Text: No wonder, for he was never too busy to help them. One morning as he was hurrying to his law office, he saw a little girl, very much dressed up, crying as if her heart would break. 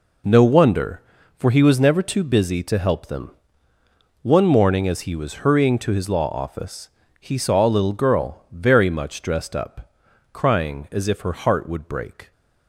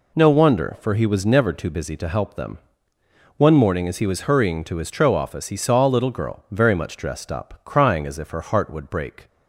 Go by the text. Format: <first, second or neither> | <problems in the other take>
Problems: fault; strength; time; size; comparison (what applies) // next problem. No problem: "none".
first | says "tro" for "law"; at 4.9 s